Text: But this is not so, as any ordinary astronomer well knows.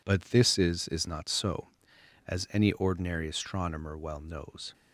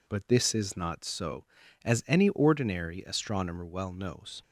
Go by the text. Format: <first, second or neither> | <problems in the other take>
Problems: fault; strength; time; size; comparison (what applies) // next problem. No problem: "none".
second | says "is" twice; at 0.8 s